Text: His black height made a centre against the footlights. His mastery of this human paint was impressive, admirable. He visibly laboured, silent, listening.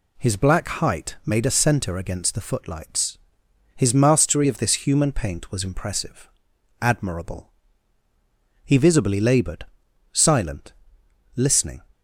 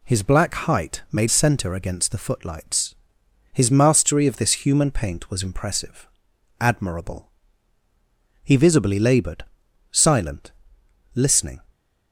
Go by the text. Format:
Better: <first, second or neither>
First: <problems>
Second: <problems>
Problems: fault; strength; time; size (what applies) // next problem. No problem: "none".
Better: first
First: none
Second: skips "a"; at 1.2 s